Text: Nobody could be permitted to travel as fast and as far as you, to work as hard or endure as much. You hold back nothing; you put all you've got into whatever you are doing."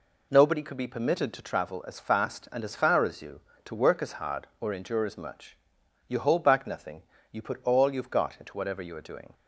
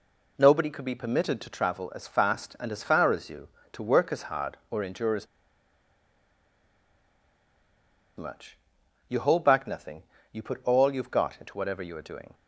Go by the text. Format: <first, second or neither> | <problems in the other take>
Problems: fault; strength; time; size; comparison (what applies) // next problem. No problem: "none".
first | pauses between "as" and "much"; strong; at 5.2 s; 2.9 s long